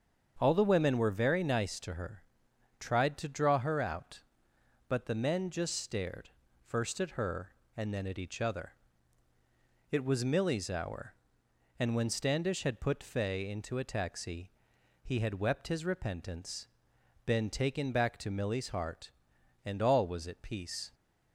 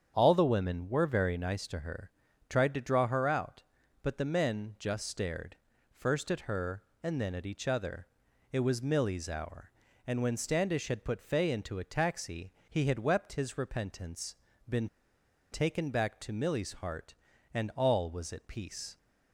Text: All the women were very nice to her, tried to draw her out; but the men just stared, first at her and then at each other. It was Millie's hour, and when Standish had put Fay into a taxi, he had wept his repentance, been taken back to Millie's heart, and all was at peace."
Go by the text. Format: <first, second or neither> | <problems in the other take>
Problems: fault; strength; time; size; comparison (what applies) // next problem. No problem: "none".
first | starts louder than the rest; strong; until 1.1 s; 8 dB; strong in the first // pauses between "been" and "taken"; noticeable; at 14.8 s; 0.64 s long